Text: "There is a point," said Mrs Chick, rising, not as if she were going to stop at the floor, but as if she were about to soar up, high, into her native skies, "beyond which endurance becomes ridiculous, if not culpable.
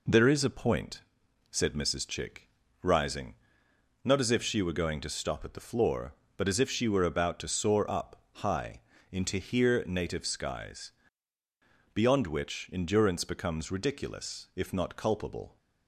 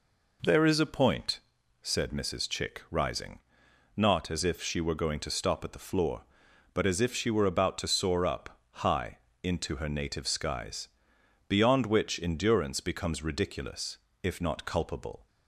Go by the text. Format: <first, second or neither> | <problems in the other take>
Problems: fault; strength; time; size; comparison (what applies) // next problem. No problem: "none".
second | says "here" for "her"; at 9.3 s